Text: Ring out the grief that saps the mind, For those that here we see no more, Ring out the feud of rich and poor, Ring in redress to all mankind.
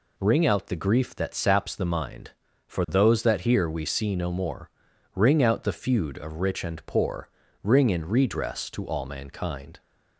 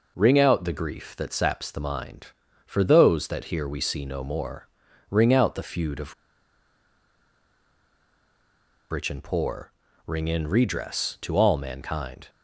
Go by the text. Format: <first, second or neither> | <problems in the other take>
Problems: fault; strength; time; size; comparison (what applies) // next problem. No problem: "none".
first | pauses between "of" and "rich"; strong; at 6.1 s; 2.7 s long